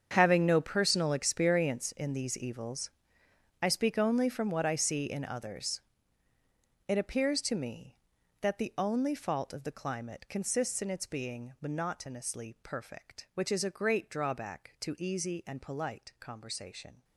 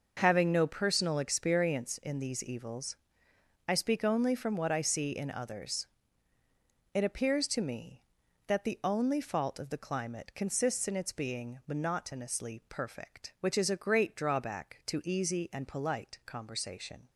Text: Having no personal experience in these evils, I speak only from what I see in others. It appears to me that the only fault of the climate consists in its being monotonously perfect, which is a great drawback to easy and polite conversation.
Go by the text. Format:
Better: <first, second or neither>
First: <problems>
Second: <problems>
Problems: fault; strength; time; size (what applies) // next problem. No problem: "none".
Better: second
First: gets quieter; strong; throughout; 14.5 dB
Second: none